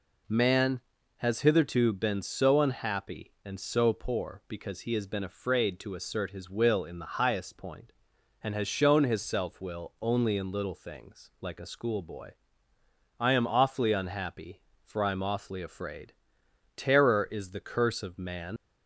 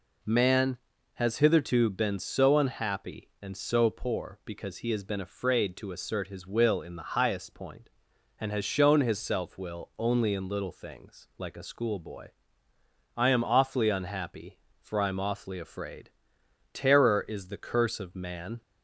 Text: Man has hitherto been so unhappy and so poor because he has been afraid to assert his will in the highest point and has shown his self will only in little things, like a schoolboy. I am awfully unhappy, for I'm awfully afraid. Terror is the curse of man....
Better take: second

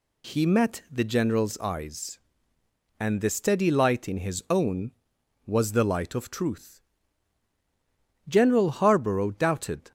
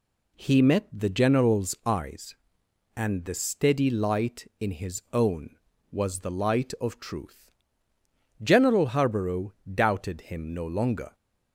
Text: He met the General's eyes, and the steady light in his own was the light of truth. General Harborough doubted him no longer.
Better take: second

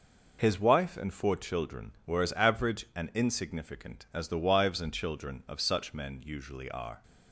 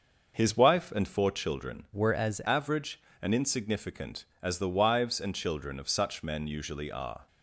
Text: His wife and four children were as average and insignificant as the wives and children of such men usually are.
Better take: first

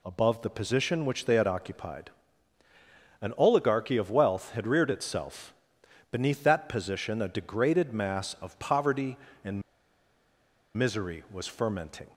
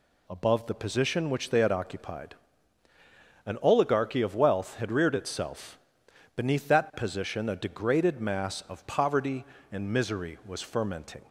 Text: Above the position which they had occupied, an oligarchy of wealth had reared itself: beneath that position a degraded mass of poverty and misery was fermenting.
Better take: second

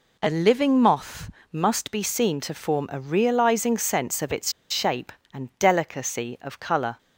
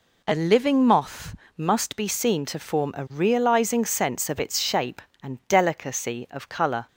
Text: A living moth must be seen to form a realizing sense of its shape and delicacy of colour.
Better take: second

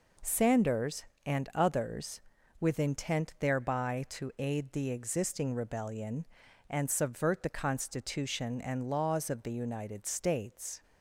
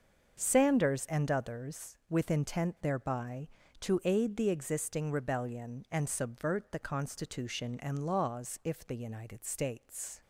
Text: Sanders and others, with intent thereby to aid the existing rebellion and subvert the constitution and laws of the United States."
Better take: first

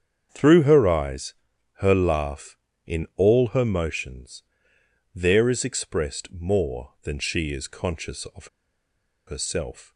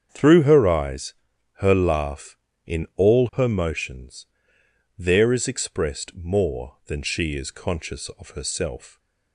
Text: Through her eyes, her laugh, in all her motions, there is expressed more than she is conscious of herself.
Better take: second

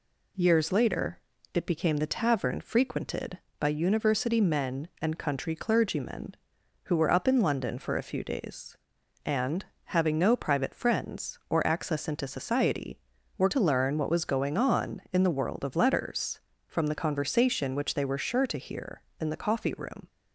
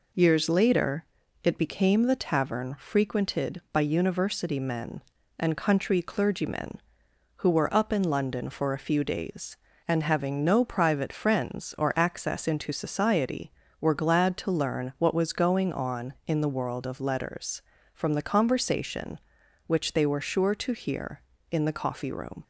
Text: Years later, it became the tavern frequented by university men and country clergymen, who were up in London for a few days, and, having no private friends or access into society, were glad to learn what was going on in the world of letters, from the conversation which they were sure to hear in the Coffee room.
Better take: second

